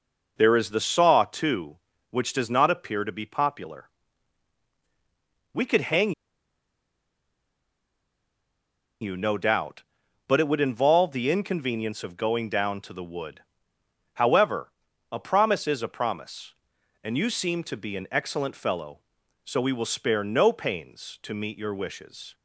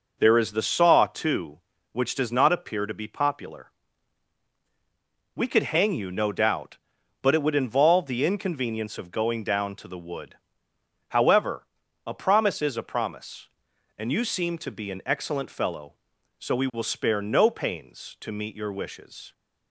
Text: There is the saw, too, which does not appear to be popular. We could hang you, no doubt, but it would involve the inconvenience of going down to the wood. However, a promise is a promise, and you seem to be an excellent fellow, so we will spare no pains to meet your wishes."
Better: second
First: pauses between "hang" and "you"; strong; at 6.1 s; 2.9 s long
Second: none

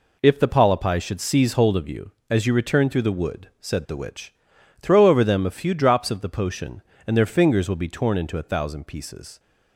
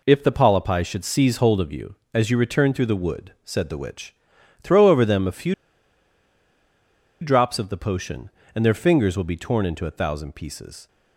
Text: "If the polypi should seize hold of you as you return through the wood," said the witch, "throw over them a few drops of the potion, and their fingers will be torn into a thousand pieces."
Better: first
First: none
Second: pauses between "few" and "drops"; strong; at 5.5 s; 1.6 s long

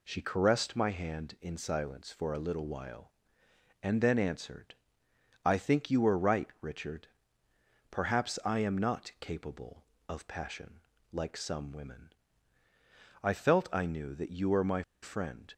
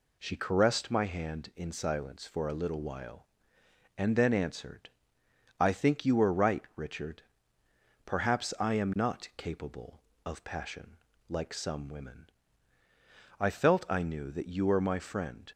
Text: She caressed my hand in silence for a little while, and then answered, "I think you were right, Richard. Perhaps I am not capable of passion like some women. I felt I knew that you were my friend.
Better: second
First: pauses between "passion" and "like"; slight; at 10.8 s; 0.30 s long // pauses between "my" and "friend"; slight; at 14.8 s; 0.19 s long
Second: pauses between "passion" and "like"; slight; at 10.9 s; 0.30 s long

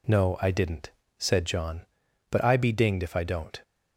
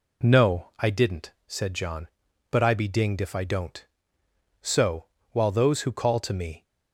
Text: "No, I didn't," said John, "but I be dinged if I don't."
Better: first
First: none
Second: goes on to say "So while those who call to me"; strong; from 4.6 s on; 2.0 s long

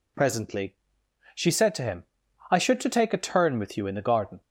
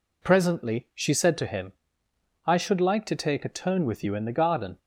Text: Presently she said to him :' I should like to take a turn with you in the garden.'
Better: second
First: pauses between "Presently" and "she"; noticeable; at 0.7 s; 0.62 s long // skips "like"; at 2.8 s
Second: none

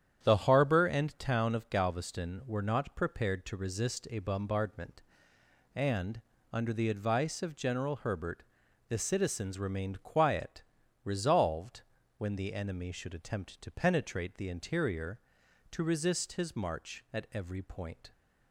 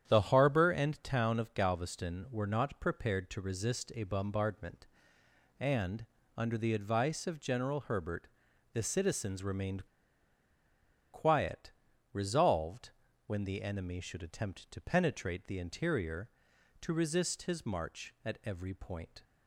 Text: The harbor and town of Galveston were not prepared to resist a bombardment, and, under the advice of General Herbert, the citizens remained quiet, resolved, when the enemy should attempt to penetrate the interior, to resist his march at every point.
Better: first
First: starts louder than the rest; strong; until 1.2 s; 9.5 dB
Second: starts louder than the rest; strong; until 1.0 s; 9.5 dB // pauses between "remained" and "quiet"; strong; at 9.8 s; 1.2 s long

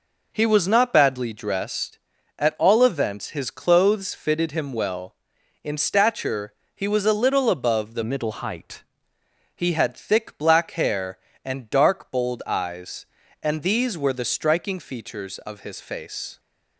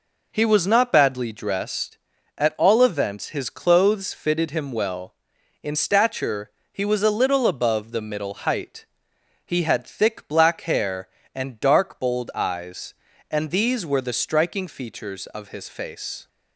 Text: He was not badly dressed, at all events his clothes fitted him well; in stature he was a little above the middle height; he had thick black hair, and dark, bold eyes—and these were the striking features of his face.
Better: second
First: pauses between "stature" and "he"; slight; at 6.5 s; 0.20 s long // changes voice from "middle" to "height"; from 8.0 to 8.8 s; 0.8 s long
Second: pauses between "stature" and "he"; slight; at 6.5 s; 0.20 s long

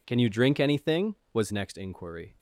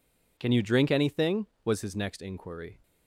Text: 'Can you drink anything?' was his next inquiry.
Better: second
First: skips "his"; at 1.5 s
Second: none

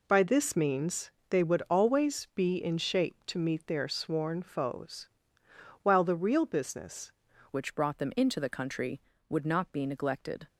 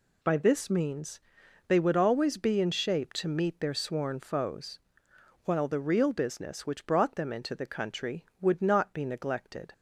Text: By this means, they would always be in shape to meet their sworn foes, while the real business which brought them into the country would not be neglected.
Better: second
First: changes voice at "which"; from 7.5 s on; 2.9 s long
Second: none

